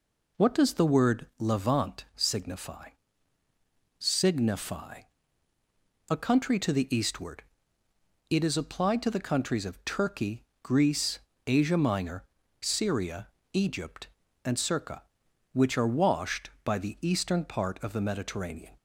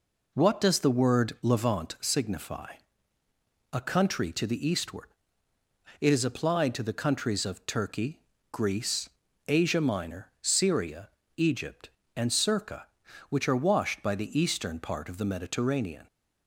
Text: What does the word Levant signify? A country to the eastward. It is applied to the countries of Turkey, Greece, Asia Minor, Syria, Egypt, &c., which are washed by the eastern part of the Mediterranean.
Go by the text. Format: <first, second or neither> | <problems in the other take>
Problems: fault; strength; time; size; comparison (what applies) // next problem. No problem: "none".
second | says "signify" twice; at 4.0 s